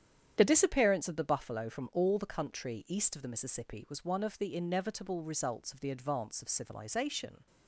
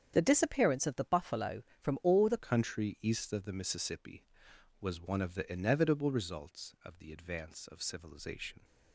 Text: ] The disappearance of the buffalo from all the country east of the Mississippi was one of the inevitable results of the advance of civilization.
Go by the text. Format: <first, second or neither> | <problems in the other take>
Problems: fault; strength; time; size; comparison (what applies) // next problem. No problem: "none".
first | starts louder than the rest; strong; until 1.1 s; 8.5 dB; strong in the first // changes voice at "country"; from 2.3 s on; 6.3 s long